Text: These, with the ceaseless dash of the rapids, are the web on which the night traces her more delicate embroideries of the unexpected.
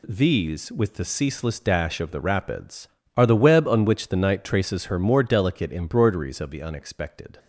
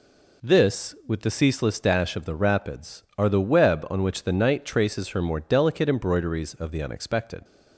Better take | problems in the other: first | says "This" for "These"; at 0.4 s

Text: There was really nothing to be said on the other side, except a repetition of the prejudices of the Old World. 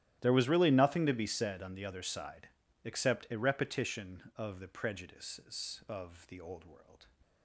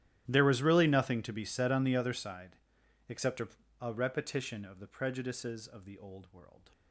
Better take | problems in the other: first | starts louder than the rest; strong; until 1.2 s; 13.5 dB; strong in the first // says "a" twice; at 3.8 s

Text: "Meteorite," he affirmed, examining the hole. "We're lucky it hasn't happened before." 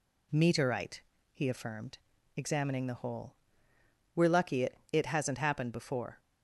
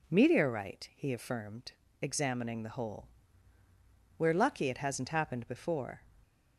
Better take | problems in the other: second | says "it" twice; at 4.9 s

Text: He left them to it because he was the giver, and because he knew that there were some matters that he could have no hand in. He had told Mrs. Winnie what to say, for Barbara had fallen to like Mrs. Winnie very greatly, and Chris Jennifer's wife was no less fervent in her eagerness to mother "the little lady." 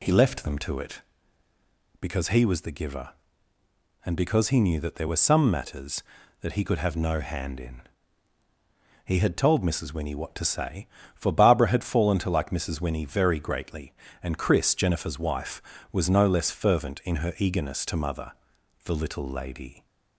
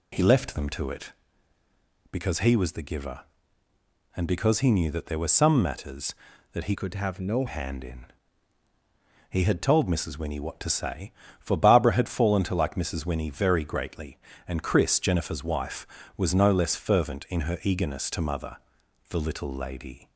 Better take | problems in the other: first | changes voice from "could" to "no"; from 6.7 to 7.4 s; 0.7 s long // pauses between "mother" and "the"; noticeable; at 18.5 s; 0.52 s long; noticeable in the first

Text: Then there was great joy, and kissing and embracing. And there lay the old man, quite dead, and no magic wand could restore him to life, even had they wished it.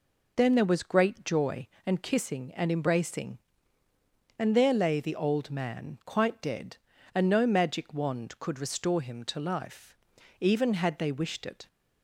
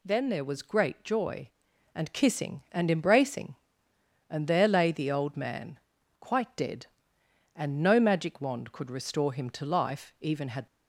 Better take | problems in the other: first | stops before "they wished it"; at 10.6 s

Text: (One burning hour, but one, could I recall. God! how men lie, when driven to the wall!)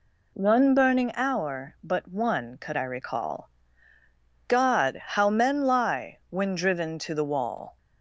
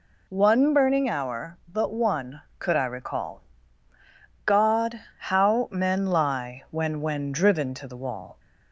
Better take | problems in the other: first | says "when" twice; at 7.0 s

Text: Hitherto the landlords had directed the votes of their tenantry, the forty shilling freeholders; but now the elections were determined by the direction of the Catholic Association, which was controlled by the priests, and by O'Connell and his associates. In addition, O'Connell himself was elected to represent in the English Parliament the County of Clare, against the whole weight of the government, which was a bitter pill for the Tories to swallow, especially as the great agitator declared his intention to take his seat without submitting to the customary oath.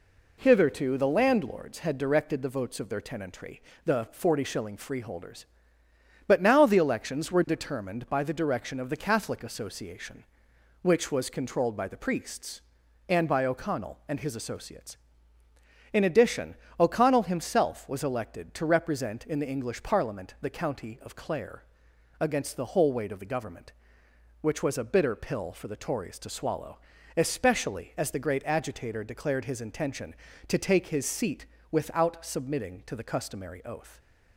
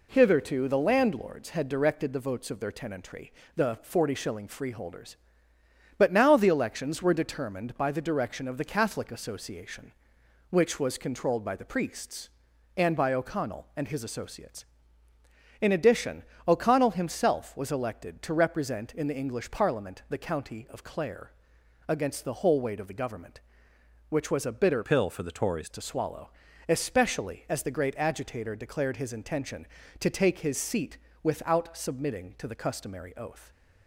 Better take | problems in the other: first | changes voice from "pill" to "Tories"; from 24.8 to 25.6 s; 0.8 s long // pauses between "seat" and "without"; slight; at 30.9 s; 0.24 s long; slight in the first

